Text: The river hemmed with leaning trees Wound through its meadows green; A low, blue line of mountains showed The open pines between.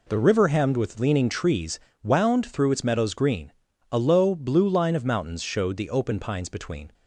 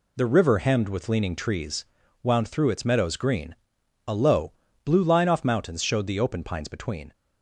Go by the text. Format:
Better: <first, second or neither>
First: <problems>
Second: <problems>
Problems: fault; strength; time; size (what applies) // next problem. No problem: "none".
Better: first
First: pauses between "trees" and "Wound"; slight; at 1.7 s; 0.22 s long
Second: pauses between "trees" and "Wound"; slight; at 1.8 s; 0.36 s long // says "off" for "of"; at 5.2 s